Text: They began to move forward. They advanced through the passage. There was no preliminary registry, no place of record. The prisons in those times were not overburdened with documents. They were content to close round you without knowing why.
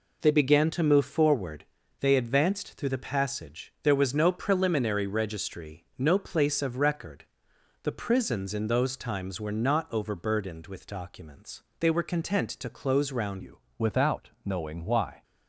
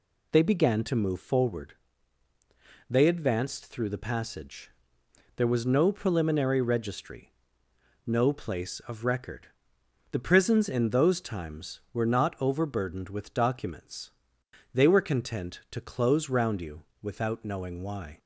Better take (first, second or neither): second